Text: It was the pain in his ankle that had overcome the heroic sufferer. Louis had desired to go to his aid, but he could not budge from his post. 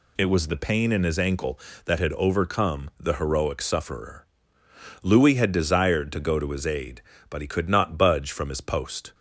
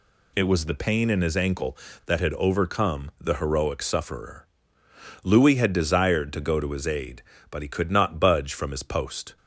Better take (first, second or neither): neither